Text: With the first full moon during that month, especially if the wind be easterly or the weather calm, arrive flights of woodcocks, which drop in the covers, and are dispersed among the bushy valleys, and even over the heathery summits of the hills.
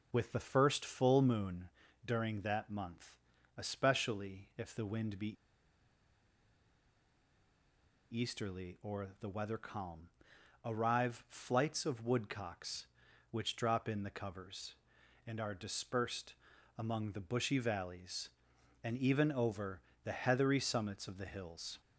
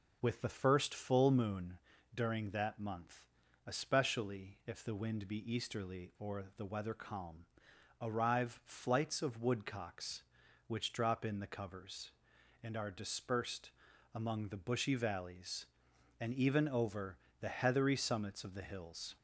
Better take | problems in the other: second | pauses between "moon" and "during"; slight; at 1.6 s; 0.36 s long; slight in the second // pauses between "be" and "easterly"; strong; at 5.2 s; 2.8 s long // pauses between "dispersed" and "among"; at 16.3 s; 0.44 s long; also in the second // pauses between "over" and "the"; slight; at 19.8 s; 0.24 s long; slight in the second

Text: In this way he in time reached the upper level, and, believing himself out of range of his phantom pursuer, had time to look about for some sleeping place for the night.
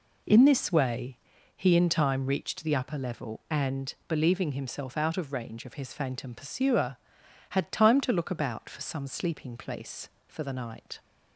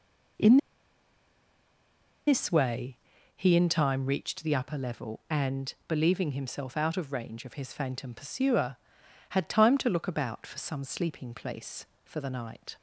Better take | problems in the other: first | pauses between "In" and "this"; strong; at 0.5 s; 1.6 s long // pauses between "way" and "he"; at 2.9 s; 0.38 s long; also in the first

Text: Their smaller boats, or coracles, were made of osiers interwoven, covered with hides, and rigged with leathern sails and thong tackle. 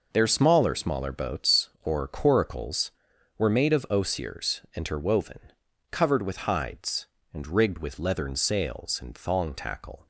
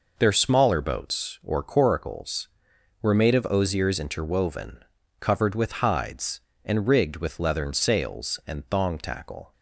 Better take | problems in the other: second | says "smaller" twice; at 0.7 s

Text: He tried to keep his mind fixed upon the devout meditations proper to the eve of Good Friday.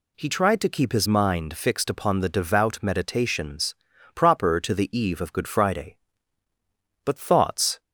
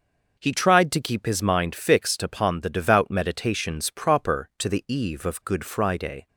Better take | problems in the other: second | pauses between "meditations" and "proper"; at 3.7 s; 0.40 s long // goes on to say "But thoughts"; noticeable; from 7.0 s on; 0.74 s long

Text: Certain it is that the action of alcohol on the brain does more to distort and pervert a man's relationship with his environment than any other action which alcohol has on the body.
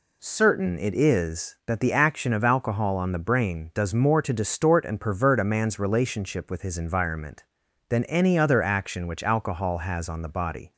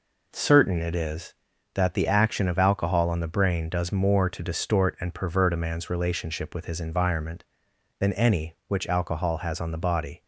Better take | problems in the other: first | skips "other action"; at 8.6 s

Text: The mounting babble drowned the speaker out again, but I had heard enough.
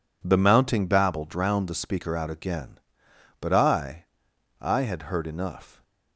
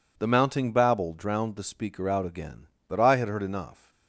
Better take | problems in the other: second | says "I" twice; at 4.6 s

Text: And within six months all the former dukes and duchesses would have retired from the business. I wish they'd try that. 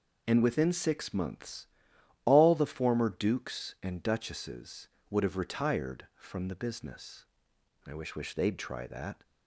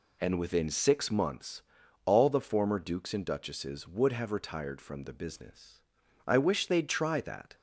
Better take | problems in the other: second | pauses between "months" and "all"; noticeable; at 1.6 s; 0.58 s long; also in the second // says "wish" twice; at 8.1 s

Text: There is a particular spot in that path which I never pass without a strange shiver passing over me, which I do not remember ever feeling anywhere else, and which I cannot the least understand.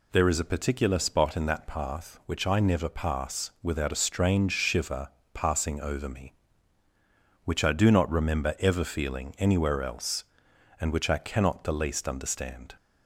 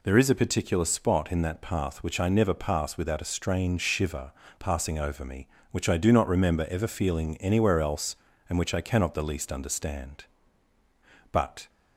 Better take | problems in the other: first | pauses between "shiver" and "passing"; slight; at 4.3 s; 0.30 s long; slight in the first // goes on to say "But"; slight; from 11.3 s on; 0.36 s long

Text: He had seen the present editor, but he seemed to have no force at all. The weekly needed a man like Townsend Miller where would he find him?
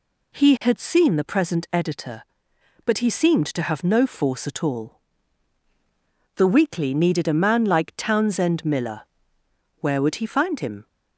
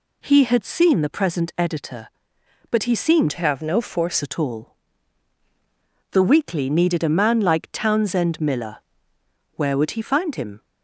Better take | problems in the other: first | changes voice from "to" to "force"; from 3.3 to 4.2 s; 0.9 s long // pauses between "Miller" and "where"; noticeable; at 8.7 s; 0.78 s long; noticeable in the first

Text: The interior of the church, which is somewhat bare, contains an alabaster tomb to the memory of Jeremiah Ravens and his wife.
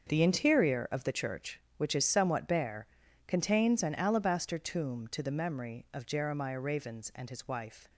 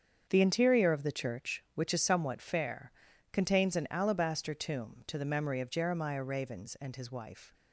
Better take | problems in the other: first | starts louder than the rest; strong; until 1.3 s; 7.5 dB; also in the first // says "fair" for "bare"; at 2.4 s

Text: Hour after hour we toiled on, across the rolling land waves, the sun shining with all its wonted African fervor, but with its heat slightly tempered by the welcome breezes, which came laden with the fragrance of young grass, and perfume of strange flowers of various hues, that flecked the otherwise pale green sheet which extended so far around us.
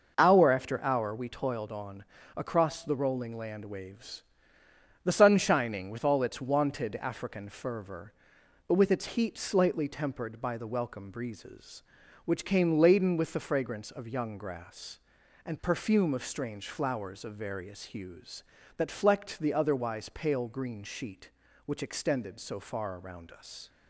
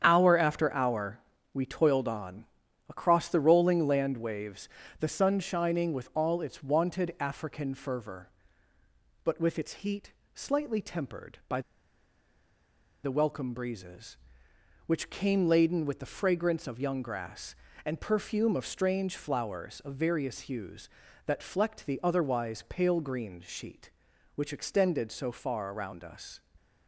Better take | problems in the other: first | starts louder than the rest; strong; until 1.0 s; 8.5 dB // pauses between "hour" and "we"; slight; at 1.2 s; 0.32 s long // pauses between "heat" and "slightly"; slight; at 10.1 s; 0.24 s long // pauses between "by" and "the"; strong; at 11.6 s; 1.4 s long

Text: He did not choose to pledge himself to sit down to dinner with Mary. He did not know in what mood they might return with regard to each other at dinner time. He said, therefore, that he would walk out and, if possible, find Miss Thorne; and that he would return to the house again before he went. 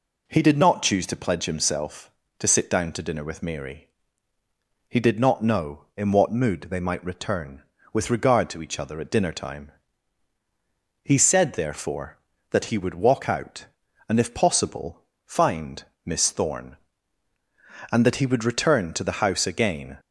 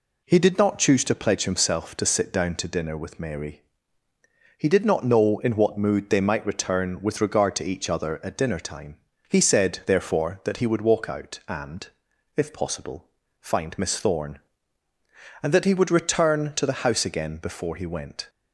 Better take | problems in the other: second | pauses between "find" and "Miss"; slight; at 15.8 s; 0.20 s long // stops before "before he went"; at 19.9 s

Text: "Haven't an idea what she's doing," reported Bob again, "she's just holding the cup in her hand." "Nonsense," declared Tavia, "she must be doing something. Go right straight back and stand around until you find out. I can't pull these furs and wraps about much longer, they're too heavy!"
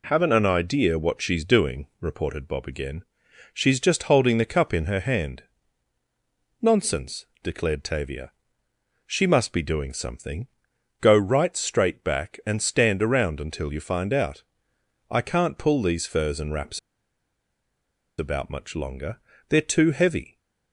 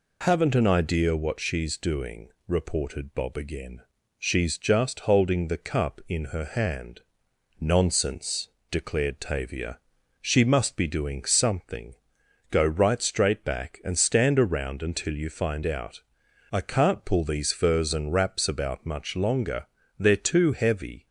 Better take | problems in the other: second | pauses between "wraps" and "about"; strong; at 16.7 s; 1.3 s long

